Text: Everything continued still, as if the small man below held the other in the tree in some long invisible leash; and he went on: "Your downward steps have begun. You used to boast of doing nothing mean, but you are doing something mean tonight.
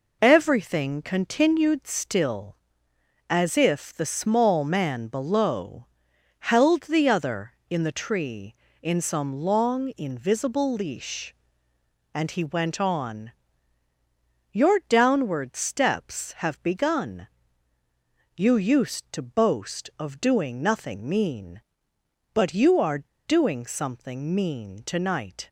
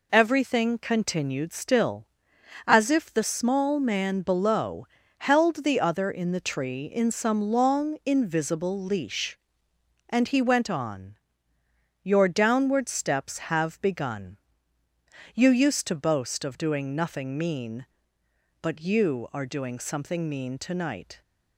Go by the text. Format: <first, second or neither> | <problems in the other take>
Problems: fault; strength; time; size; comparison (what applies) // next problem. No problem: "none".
second | pauses between "below" and "held"; noticeable; at 5.8 s; 0.54 s long; slight in the second // pauses between "are" and "doing"; slight; at 23.0 s; 0.21 s long